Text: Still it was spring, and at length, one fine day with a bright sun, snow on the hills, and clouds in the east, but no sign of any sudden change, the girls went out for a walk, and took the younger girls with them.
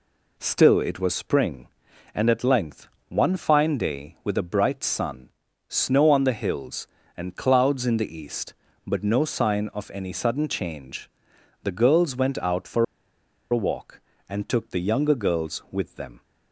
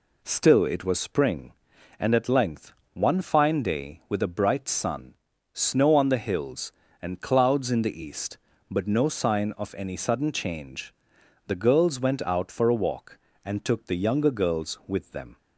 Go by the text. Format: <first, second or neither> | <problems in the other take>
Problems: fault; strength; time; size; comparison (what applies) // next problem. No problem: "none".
second | pauses between "for" and "a"; noticeable; at 12.8 s; 0.66 s long